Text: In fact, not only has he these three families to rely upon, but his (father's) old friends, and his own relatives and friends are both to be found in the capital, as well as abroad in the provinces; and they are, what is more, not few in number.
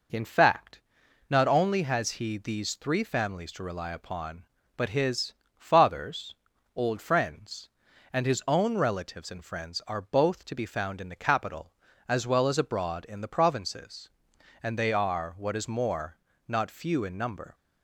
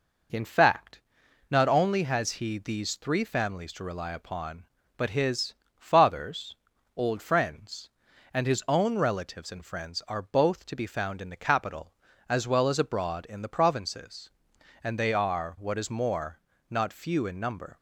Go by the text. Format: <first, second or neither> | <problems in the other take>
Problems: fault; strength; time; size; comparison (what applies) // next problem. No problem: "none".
neither | none